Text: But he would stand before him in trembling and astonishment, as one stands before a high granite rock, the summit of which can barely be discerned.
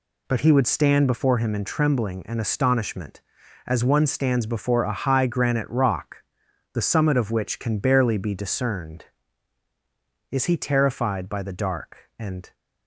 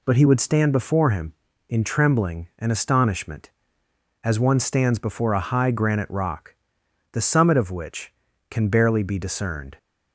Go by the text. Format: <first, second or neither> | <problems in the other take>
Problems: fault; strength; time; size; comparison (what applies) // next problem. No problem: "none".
second | goes on to say "Is he terrified by the dark and"; strong; from 10.3 s on; 2.2 s long